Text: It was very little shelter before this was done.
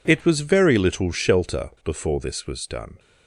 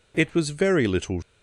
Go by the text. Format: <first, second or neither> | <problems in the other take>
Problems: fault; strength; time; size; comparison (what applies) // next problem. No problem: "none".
first | stops before "shelter before this was done"; at 1.2 s